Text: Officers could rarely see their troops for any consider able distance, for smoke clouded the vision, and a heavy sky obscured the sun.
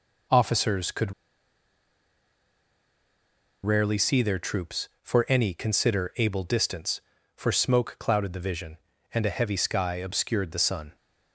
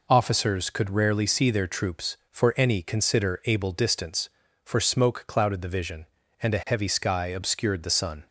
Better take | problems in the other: second | pauses between "could" and "rarely"; strong; at 1.1 s; 2.5 s long

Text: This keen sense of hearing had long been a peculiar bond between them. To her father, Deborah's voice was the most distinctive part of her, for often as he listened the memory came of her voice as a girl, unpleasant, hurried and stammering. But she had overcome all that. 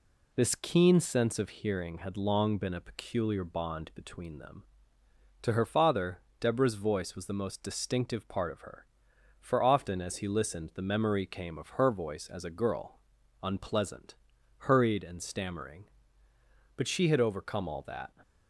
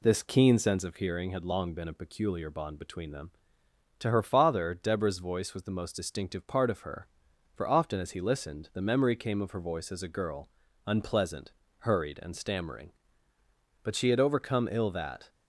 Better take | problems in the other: first | says "ill" for "all"; at 14.6 s

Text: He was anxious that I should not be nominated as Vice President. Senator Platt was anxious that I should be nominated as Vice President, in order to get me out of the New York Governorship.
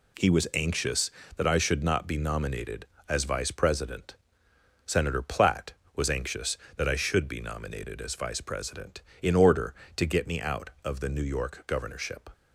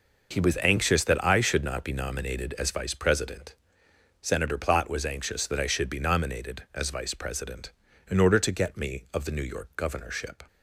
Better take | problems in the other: first | skips "out"; at 9.0 s

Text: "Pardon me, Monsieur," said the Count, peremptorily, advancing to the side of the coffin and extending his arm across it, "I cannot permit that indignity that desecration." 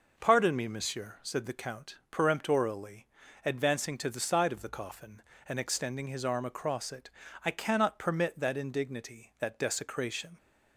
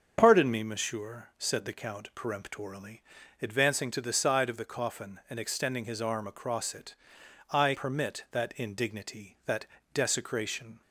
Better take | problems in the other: first | starts louder than the rest; until 1.2 s; 7 dB // skips "cannot"; at 7.7 s // pauses between "that" and "desecration"; slight; at 9.6 s; 0.26 s long

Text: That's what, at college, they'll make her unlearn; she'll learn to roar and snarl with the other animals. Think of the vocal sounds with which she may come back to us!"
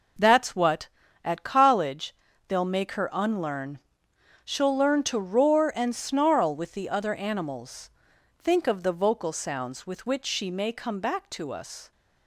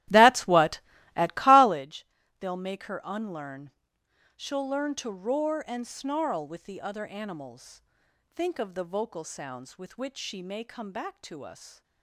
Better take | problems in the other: first | starts louder than the rest; strong; until 1.8 s; 14 dB

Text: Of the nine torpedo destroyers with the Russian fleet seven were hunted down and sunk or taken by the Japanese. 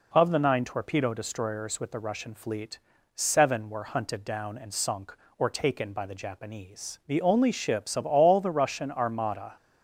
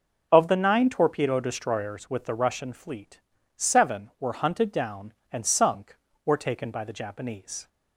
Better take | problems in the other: second | pauses between "fleet" and "seven"; slight; at 2.7 s; 0.36 s long; slight in the second // goes on to say "The only ships of all the Russian armada"; strong; from 7.0 s on; 2.4 s long

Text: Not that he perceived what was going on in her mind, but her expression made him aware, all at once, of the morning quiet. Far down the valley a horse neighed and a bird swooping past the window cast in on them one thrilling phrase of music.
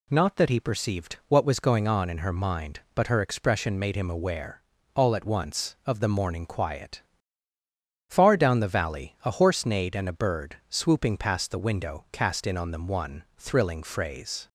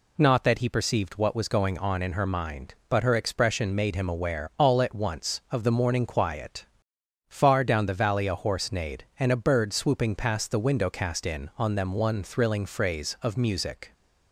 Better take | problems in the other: second | stops before "of music"; at 14.4 s

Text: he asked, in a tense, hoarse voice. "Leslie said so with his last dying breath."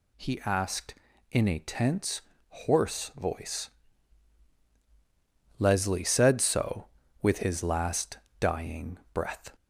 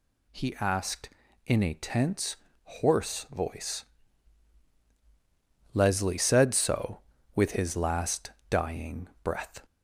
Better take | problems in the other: neither | pauses between "last" and "dying"; slight; the same in both // pauses between "dying" and "breath"; slight; the same in both

